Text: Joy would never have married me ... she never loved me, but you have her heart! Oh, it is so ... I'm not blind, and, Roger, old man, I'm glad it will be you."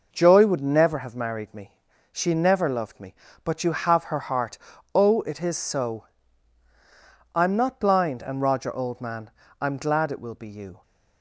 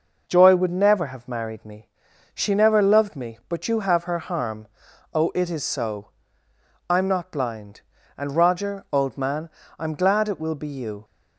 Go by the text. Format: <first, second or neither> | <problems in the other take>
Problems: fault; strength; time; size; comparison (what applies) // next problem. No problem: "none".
first | says "harm" for "heart"; at 4.1 s